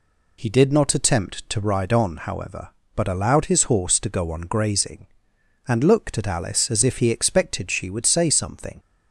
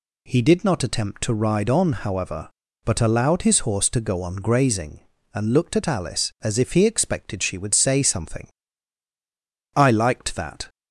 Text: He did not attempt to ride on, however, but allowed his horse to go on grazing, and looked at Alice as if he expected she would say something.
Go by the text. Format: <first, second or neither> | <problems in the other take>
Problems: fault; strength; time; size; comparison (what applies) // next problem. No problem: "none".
first | goes on to say "I liked that"; noticeable; from 9.7 s on; 0.92 s long